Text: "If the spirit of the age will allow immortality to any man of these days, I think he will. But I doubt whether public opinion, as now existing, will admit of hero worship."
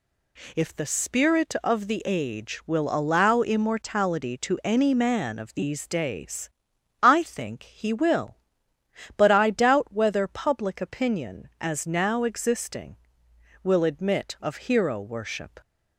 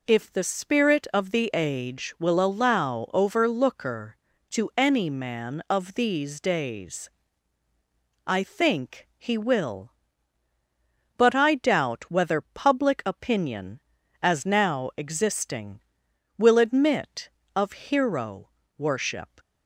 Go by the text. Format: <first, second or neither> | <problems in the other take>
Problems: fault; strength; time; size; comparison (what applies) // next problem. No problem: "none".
first | says "overlooker" for "immortality"; at 3.1 s // pauses between "hero" and "worship"; slight; at 18.4 s; 0.28 s long